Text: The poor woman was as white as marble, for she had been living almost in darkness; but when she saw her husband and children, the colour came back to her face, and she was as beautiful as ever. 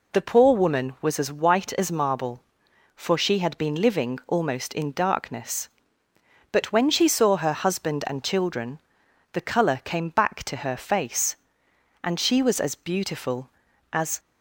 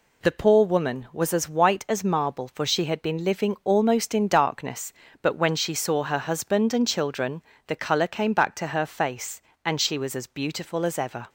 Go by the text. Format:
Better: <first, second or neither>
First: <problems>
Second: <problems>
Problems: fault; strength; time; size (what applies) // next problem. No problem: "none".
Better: second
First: stops before "ever"; at 14.1 s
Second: none